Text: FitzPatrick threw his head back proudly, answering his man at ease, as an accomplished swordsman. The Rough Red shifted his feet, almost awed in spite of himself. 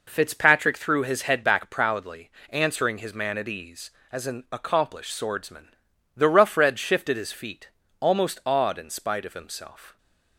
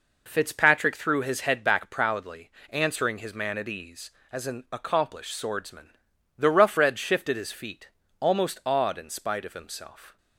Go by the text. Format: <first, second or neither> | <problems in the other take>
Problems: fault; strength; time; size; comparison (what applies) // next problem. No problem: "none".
neither | none